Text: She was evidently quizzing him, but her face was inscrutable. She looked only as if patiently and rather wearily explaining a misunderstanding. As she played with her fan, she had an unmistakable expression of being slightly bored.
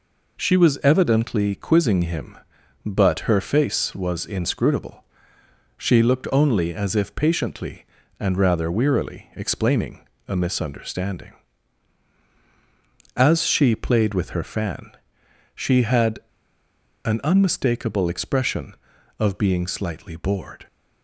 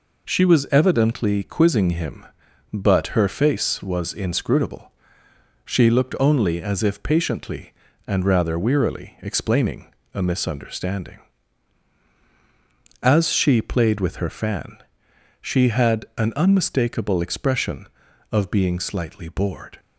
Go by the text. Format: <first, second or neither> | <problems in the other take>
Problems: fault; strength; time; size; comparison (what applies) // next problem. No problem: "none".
second | pauses between "explaining" and "a"; slight; at 10.0 s; 0.22 s long; slight in the second // pauses between "had" and "an"; noticeable; at 16.1 s; 0.84 s long